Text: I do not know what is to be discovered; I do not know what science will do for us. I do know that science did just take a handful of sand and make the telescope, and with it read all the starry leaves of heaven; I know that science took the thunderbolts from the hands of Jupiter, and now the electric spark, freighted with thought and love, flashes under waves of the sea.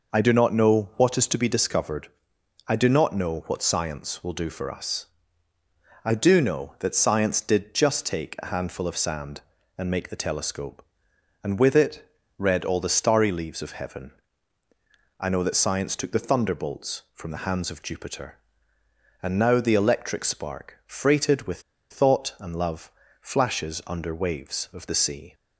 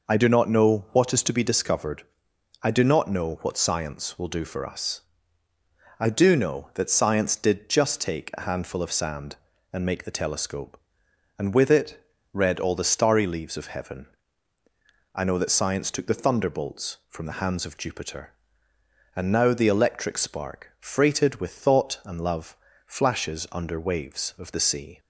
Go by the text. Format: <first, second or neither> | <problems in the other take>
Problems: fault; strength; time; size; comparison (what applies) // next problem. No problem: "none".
second | pauses between "it" and "read"; slight; at 12.1 s; 0.28 s long; slight in the second // pauses between "with" and "thought"; slight; at 21.6 s; 0.30 s long